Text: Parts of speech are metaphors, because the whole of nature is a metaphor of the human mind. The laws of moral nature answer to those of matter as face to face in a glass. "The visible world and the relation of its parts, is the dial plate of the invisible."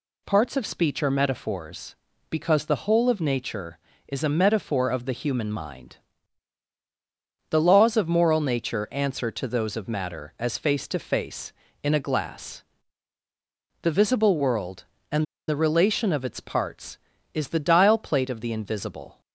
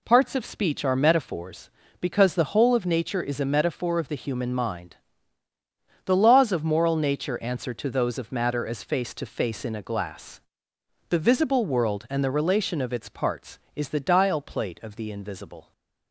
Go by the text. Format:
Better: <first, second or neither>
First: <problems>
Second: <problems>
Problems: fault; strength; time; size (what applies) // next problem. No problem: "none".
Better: second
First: pauses between "and" and "the"; slight; at 15.2 s; 0.23 s long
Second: none